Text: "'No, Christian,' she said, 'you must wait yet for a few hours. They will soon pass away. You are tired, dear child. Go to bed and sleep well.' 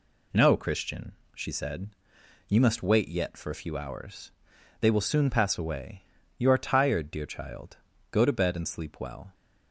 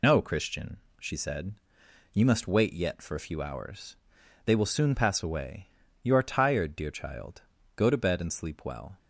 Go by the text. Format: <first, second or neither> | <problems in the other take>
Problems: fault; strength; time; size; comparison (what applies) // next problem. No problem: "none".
first | loses the start of "No"; at 0.0 s; 70 ms